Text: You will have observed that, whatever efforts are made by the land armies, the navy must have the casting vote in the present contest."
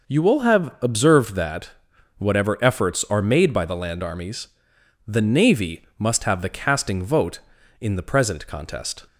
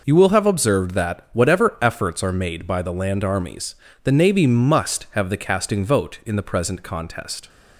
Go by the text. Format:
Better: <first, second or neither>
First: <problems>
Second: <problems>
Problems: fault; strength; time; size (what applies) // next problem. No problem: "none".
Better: neither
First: none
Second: none